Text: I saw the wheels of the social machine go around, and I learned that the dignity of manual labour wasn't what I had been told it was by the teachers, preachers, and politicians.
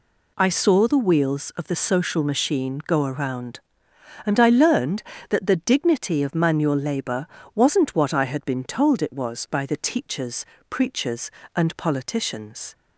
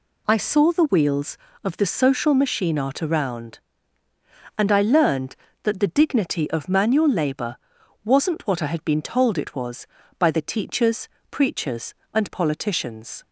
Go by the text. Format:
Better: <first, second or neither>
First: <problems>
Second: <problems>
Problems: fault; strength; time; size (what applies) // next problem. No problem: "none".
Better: first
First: pauses between "labour" and "wasn't"; slight; at 7.2 s; 0.26 s long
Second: says "art" for "go"; at 2.7 s // pauses between "labour" and "wasn't"; noticeable; at 7.5 s; 0.48 s long